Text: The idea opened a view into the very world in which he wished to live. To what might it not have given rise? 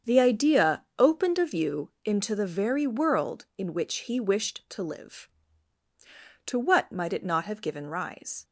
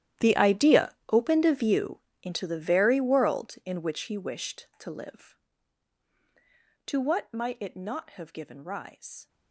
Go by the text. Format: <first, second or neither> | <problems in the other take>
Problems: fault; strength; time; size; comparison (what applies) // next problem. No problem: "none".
first | gets quieter; strong; throughout; 18.5 dB // starts louder than the rest; strong; until 1.3 s; 11.5 dB; strong in the first // pauses between "idea" and "opened"; slight; at 0.9 s; 0.18 s long // pauses between "view" and "into"; slight; at 1.9 s; 0.22 s long